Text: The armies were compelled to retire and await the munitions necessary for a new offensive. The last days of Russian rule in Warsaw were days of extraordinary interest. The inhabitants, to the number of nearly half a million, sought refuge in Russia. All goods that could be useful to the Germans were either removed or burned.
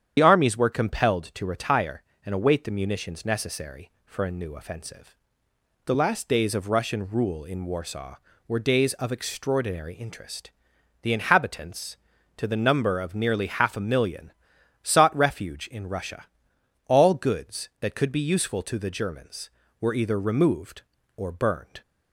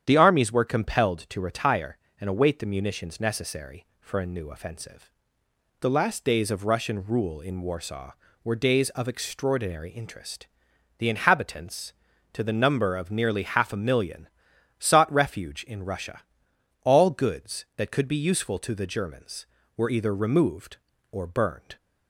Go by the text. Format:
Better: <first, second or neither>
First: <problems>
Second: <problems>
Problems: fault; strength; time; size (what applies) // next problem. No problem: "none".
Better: second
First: loses the start of "The"; at 0.1 s; 50 ms // starts louder than the rest; strong; until 1.1 s; 9 dB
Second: starts louder than the rest; strong; until 1.0 s; 9 dB